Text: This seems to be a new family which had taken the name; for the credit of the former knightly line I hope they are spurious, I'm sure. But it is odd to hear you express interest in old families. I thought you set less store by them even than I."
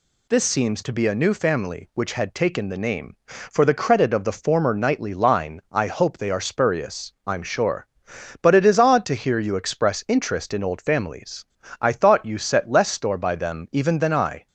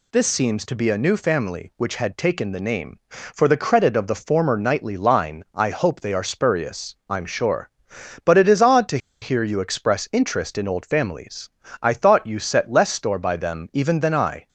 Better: first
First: none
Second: pauses between "to" and "hear"; slight; at 8.9 s; 0.23 s long

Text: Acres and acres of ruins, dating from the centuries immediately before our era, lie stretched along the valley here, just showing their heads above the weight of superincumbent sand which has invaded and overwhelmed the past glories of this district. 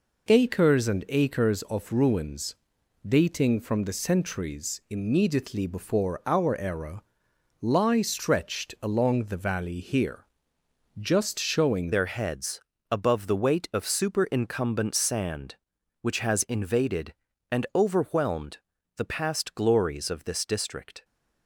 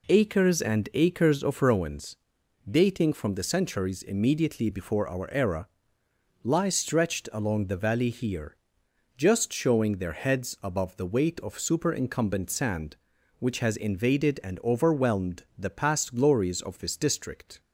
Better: second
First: changes voice at "their"; from 11.9 s on; 9.1 s long // pauses between "heads" and "above"; slight; at 12.6 s; 0.30 s long // pauses between "overwhelmed" and "the"; at 18.5 s; 0.40 s long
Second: none

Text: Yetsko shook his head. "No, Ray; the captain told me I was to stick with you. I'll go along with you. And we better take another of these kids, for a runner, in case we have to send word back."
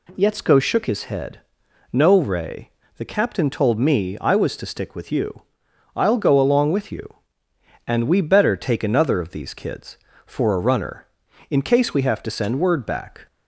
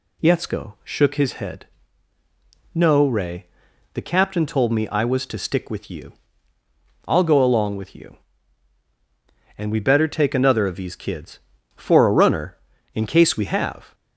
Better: first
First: none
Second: stops before "to send word back"; at 13.9 s

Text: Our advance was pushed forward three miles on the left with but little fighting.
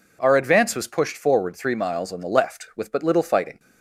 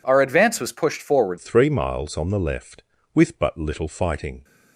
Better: first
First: none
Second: changes voice at "three"; from 1.3 s on; 3.1 s long

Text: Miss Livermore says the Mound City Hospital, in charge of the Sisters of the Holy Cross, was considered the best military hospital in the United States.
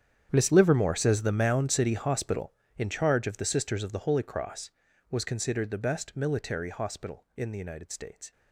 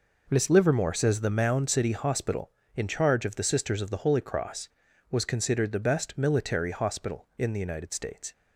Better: second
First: gets quieter; strong; throughout; 17.5 dB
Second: none

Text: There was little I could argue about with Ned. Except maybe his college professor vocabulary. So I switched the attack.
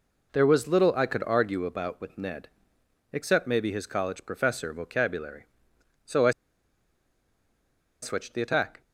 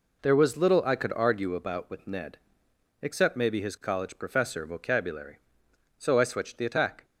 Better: second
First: pauses between "I" and "switched"; strong; at 6.3 s; 1.7 s long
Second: none

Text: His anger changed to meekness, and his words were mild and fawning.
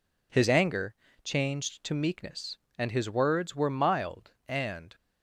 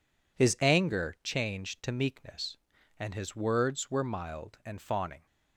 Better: second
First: pauses between "anger" and "changed"; slight; at 0.9 s; 0.30 s long // stops before "fawning"; at 4.9 s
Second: none

